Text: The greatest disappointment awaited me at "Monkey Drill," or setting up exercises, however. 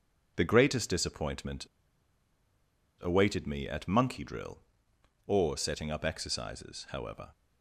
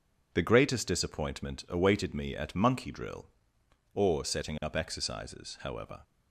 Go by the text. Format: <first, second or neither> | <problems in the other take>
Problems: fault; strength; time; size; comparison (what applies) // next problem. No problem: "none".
second | pauses between "disappointment" and "awaited"; strong; at 1.6 s; 1.3 s long